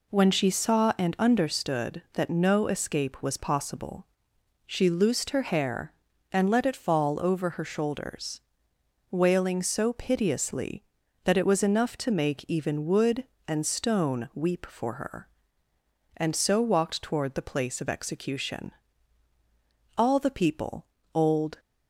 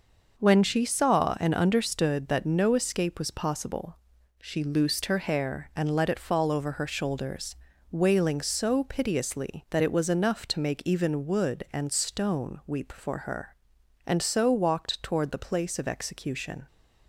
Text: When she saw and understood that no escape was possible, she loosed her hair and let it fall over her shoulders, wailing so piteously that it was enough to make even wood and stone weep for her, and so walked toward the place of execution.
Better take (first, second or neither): second